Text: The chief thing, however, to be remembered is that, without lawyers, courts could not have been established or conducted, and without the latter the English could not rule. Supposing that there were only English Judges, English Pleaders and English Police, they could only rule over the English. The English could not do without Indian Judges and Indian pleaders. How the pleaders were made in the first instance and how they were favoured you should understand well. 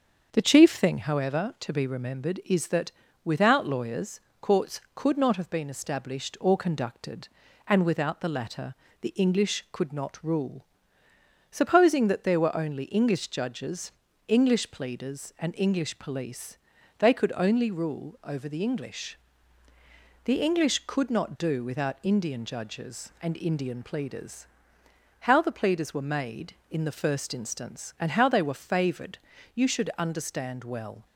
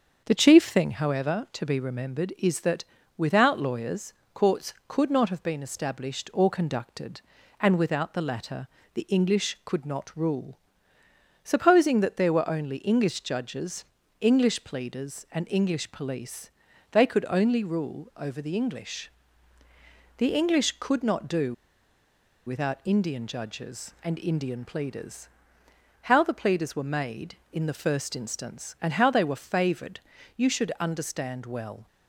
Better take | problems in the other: first | starts louder than the rest; until 1.2 s; 7 dB; also in the first // pauses between "latter" and "the"; slight; at 8.6 s; 0.26 s long; slight in the first // pauses between "do" and "without"; noticeable; at 21.5 s; 0.91 s long // pauses between "favoured" and "you"; slight; at 30.0 s; 0.36 s long; slight in the first

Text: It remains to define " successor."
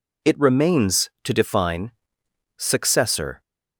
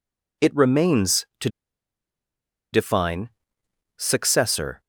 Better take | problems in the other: first | pauses between "to" and "define"; at 1.4 s; 1.2 s long

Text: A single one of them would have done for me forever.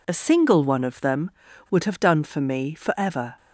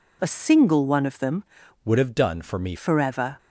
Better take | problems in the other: first | changes voice from "would" to "me"; from 1.8 to 2.7 s; 0.9 s long

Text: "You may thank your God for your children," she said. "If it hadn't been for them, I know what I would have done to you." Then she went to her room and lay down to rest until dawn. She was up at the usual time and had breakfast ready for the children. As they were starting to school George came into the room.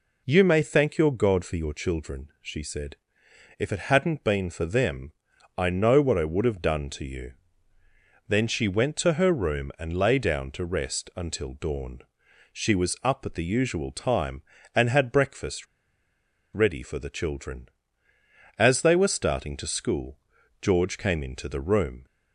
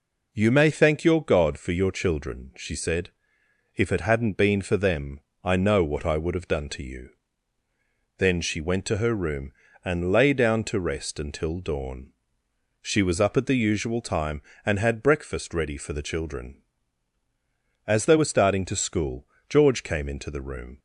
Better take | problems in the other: second | pauses between "breakfast" and "ready"; noticeable; at 15.6 s; 0.89 s long // pauses between "school" and "George"; at 20.1 s; 0.44 s long; slight in the second

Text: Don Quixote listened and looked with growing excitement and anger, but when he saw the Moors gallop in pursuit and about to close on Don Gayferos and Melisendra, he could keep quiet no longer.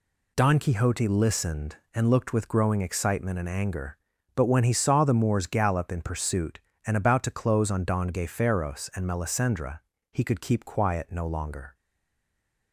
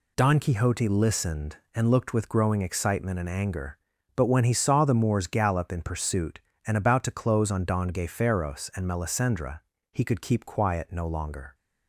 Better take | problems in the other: second | stays silent after the last word; from 11.7 s on; 1.0 s long

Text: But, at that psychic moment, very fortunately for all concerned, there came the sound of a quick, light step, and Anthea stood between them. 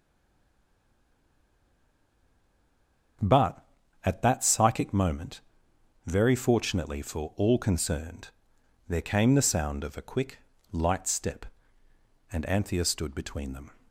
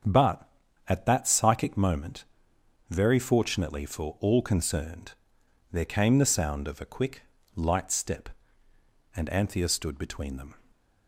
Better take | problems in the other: second | stays silent before the first word; strong; until 3.1 s; 3.1 s long // starts louder than the rest; until 4.6 s; 7 dB; also in the second

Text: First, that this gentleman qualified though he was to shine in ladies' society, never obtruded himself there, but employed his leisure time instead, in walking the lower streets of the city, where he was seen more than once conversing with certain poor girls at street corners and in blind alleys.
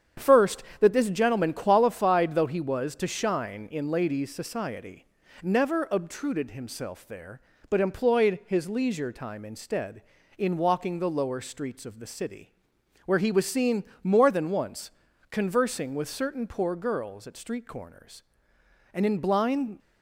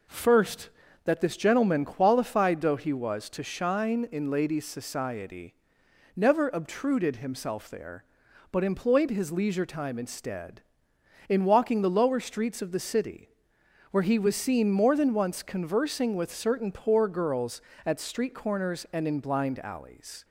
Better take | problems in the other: second | starts louder than the rest; strong; until 1.3 s; 8.5 dB // pauses between "seen" and "more"; slight; at 13.8 s; 0.18 s long // pauses between "once" and "conversing"; at 14.9 s; 0.40 s long // stops before "alleys"; at 19.7 s

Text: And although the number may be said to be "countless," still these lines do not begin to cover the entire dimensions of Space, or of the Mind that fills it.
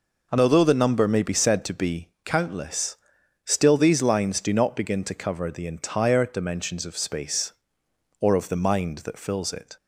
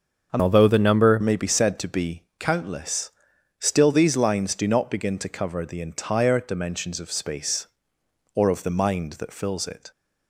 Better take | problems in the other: first | starts louder than the rest; until 1.3 s; 6.5 dB // changes voice from "although" to "number"; from 0.4 to 1.2 s; 0.8 s long // pauses between "be" and "countless"; slight; at 2.2 s; 0.16 s long; slight in the first

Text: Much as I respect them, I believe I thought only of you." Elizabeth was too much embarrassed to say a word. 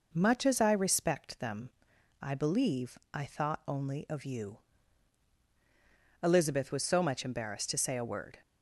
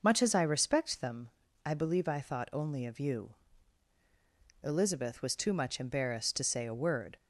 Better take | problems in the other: second | pauses between "believe" and "I"; slight; at 2.9 s; 0.16 s long // says "so" for "too"; at 6.8 s

